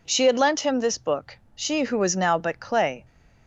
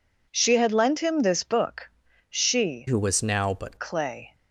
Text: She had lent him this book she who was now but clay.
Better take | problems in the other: first | pauses between "book" and "she"; at 1.8 s; 0.40 s long; slight in the first // changes voice from "who" to "but"; from 2.8 to 3.7 s; 0.9 s long

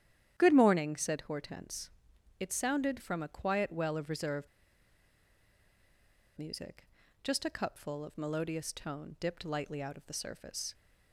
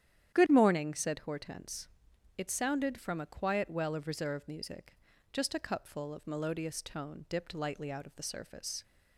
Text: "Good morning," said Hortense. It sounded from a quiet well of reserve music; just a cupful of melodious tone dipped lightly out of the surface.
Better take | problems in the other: second | starts louder than the rest; strong; until 1.3 s; 10.5 dB; strong in the second // pauses between "reserve" and "music"; strong; at 4.4 s; 1.9 s long

